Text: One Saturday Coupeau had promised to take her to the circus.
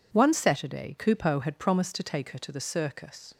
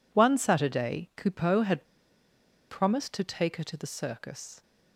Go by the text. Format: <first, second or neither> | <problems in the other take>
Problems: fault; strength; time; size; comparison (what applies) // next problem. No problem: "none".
first | pauses between "had" and "promised"; noticeable; at 1.8 s; 0.84 s long